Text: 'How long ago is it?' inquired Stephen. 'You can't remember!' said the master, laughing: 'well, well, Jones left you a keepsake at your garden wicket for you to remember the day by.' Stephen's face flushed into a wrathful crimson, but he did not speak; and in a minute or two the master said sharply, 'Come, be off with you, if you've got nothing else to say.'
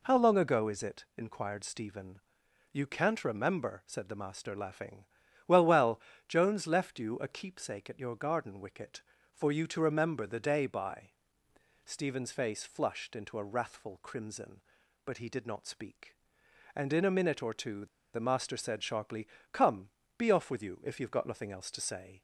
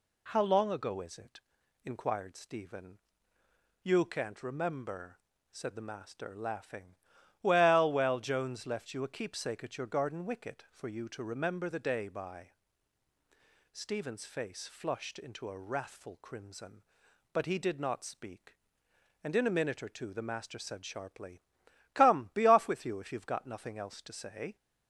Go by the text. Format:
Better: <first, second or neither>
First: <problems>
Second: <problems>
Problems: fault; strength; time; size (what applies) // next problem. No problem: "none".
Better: second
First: pauses between "two" and "the"; slight; at 17.8 s; 0.28 s long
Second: none